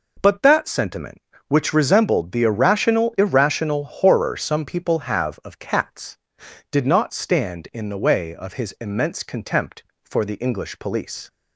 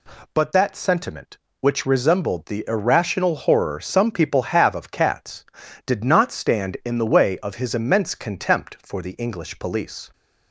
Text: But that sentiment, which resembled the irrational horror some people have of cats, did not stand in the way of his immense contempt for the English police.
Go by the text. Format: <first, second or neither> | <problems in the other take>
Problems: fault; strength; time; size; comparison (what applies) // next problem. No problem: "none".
second | says "irrational" twice; at 3.1 s